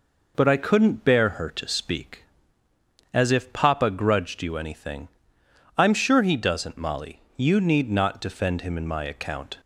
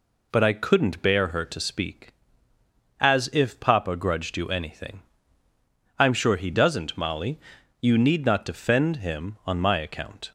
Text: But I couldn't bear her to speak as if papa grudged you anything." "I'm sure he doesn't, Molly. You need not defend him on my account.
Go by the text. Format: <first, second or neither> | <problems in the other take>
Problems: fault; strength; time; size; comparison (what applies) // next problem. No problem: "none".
second | says "in" for "on"; at 8.7 s